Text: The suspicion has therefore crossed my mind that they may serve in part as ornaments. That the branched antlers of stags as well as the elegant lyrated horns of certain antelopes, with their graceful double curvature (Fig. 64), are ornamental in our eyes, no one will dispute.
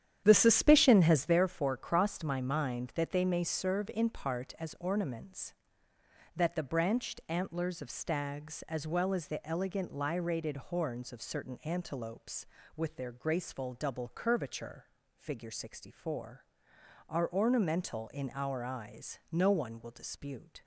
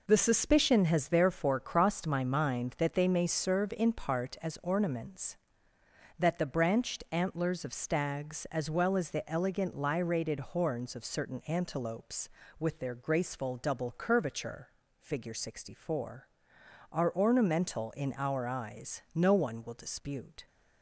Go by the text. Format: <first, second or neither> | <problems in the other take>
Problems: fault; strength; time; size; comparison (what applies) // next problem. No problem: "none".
second | starts louder than the rest; strong; until 1.4 s; 10 dB